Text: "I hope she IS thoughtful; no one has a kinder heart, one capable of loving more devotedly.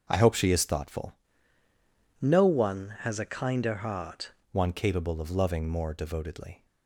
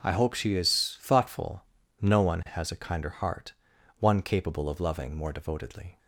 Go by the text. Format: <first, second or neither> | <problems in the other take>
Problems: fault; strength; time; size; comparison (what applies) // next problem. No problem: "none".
second | starts louder than the rest; until 1.0 s; 7 dB // changes voice from "no" to "heart"; from 2.2 to 4.3 s; 2.1 s long